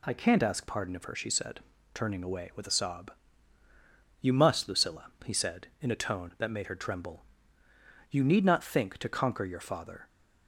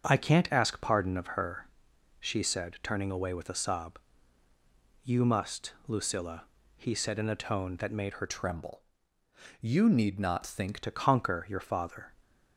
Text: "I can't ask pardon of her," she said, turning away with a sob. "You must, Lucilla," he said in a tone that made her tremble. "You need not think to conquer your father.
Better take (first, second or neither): first